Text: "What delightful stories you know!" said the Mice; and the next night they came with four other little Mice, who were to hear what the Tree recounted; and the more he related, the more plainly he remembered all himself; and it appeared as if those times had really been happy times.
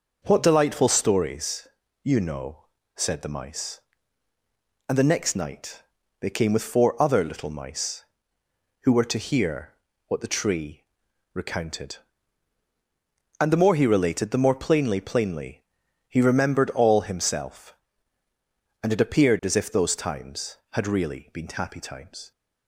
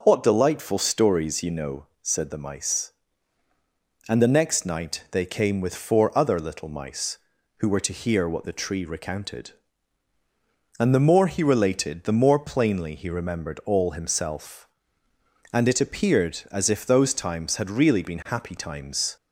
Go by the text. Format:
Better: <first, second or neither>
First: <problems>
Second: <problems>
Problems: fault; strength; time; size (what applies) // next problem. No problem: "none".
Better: second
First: pauses between "stories" and "you"; at 1.6 s; 0.38 s long // pauses between "night" and "they"; at 5.8 s; 0.38 s long // pauses between "hear" and "what"; slight; at 9.7 s; 0.32 s long // pauses between "Tree" and "recounted"; noticeable; at 10.8 s; 0.50 s long // says "plainly" twice; at 15.0 s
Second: none